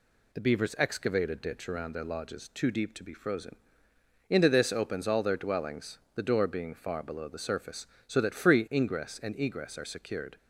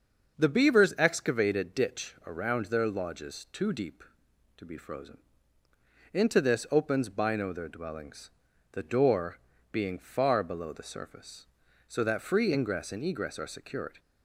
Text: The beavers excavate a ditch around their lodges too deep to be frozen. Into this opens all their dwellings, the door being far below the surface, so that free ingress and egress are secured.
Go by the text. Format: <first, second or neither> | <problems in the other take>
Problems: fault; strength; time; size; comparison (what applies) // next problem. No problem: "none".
first | starts louder than the rest; until 1.4 s; 6.5 dB // says "bino" for "all"; at 7.0 s // pauses between "door" and "being"; slight; at 9.3 s; 0.32 s long